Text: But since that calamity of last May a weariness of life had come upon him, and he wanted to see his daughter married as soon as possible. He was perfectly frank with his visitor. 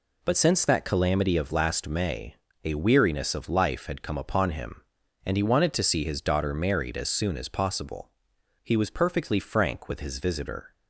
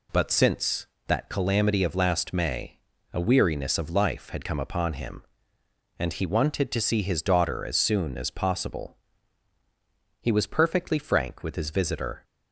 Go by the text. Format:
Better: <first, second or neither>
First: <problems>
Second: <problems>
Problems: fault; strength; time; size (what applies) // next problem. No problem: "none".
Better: first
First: pauses between "May" and "a"; slight; at 2.3 s; 0.28 s long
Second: pauses between "May" and "a"; slight; at 2.7 s; 0.36 s long // skips "married"; at 7.6 s